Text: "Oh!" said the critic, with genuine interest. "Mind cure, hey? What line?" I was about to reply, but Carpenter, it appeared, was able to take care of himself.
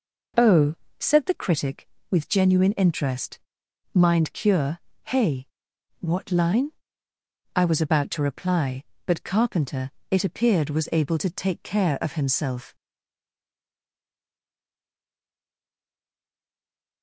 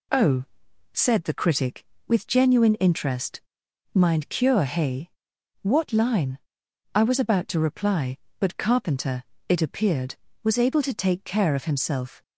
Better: second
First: stays silent after the last word; strong; from 12.7 s on; 4.3 s long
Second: none

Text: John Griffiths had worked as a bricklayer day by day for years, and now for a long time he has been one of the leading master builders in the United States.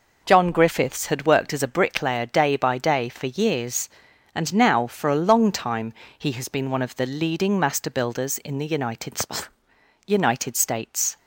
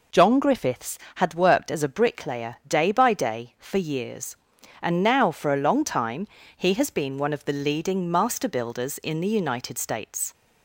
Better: second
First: pauses between "time" and "he"; slight; at 5.9 s; 0.26 s long // says "United" twice; at 10.0 s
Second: pauses between "time" and "he"; slight; at 6.2 s; 0.28 s long

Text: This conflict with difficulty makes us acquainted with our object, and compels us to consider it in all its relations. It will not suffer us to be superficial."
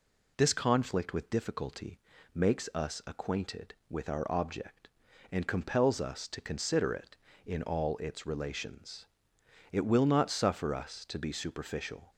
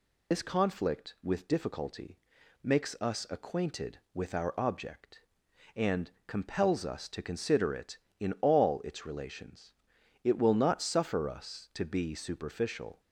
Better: first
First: pauses between "difficulty" and "makes"; slight; at 2.0 s; 0.34 s long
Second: loses the start of "This"; at 0.3 s; 110 ms // pauses between "difficulty" and "makes"; noticeable; at 2.1 s; 0.46 s long // pauses between "and" and "compels"; slight; at 6.0 s; 0.16 s long

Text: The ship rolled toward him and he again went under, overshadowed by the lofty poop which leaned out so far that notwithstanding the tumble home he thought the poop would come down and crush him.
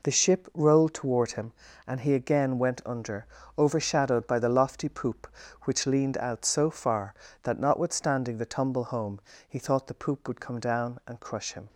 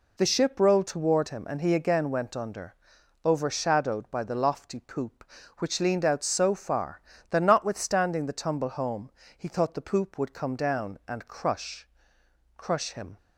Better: first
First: pauses between "home" and "he"; slight; at 9.1 s; 0.28 s long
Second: pauses between "home" and "he"; slight; at 9.1 s; 0.28 s long // says "crush" twice; at 12.5 s

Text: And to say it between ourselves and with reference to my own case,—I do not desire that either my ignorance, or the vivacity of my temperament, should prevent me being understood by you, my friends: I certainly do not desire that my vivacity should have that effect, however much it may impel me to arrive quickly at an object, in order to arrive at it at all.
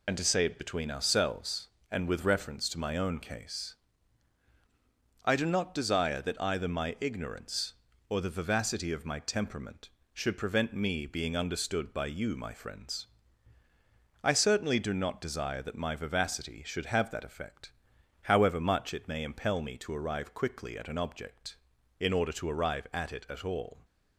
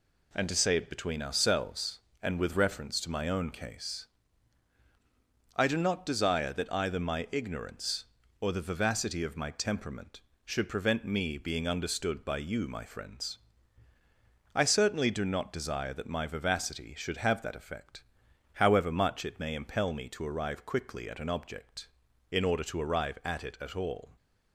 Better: second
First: loses the start of "And"; at 0.0 s; 65 ms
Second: none

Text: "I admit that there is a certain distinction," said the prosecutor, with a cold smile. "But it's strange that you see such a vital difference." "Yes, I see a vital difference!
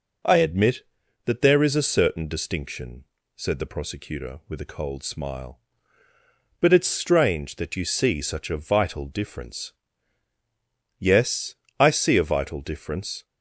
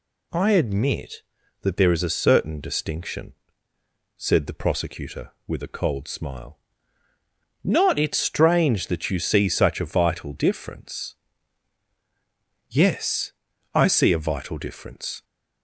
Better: first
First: none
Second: says "Not" for "But"; at 7.6 s

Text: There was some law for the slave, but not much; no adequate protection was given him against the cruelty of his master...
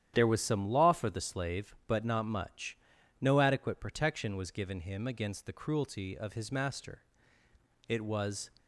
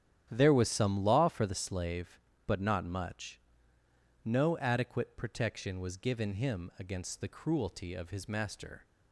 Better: second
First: starts louder than the rest; strong; until 1.1 s; 10 dB // goes on to say "It was"; noticeable; from 7.8 s on; 0.62 s long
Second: starts louder than the rest; strong; until 1.3 s; 10 dB

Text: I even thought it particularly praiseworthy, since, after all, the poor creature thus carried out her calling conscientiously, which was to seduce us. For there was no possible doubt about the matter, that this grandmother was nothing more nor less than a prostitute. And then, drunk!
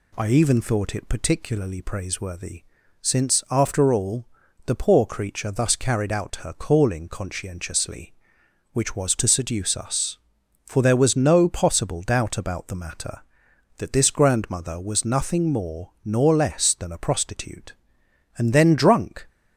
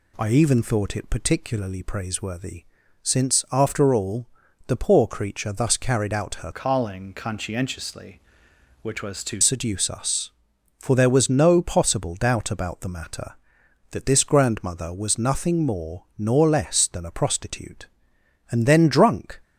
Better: first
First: none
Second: changes voice from "calling" to "to"; from 6.5 to 9.4 s; 2.9 s long

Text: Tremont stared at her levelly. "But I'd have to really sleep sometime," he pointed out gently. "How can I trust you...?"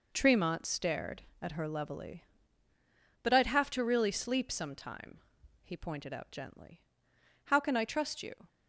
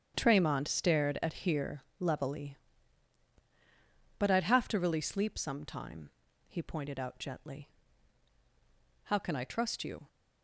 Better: first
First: none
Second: starts louder than the rest; strong; until 1.1 s; 8.5 dB // says "here" for "her"; at 1.3 s

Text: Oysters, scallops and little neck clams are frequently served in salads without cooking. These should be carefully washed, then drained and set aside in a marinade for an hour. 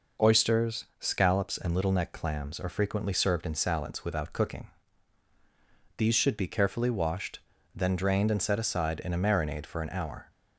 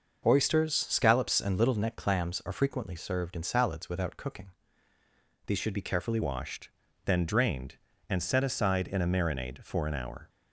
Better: first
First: none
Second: starts louder than the rest; noticeable; until 1.4 s; 6 dB // changes voice at "washed"; from 6.2 s on; 4.0 s long

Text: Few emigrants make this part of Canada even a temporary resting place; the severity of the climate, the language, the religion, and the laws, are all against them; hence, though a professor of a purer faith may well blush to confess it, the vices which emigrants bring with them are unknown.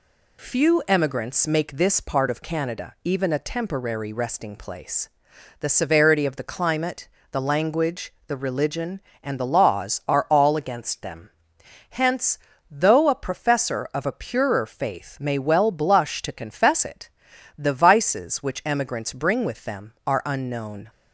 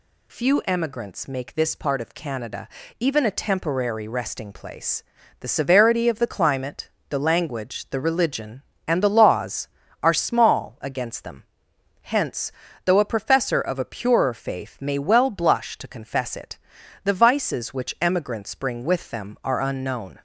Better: first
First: none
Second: pauses between "Canada" and "even"; slight; at 2.6 s; 0.32 s long // says "small" for "all"; at 10.1 s

